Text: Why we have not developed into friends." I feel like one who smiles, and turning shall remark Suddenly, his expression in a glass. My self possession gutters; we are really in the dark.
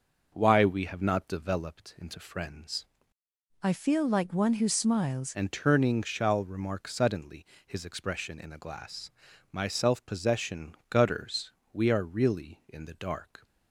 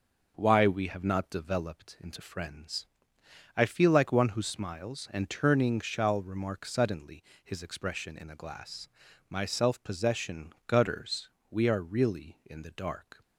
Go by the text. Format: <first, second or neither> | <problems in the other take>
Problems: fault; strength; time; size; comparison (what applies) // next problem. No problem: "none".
second | starts louder than the rest; noticeable; until 1.3 s; 6 dB // changes voice from "I" to "smiles"; from 3.6 to 5.3 s; 1.7 s long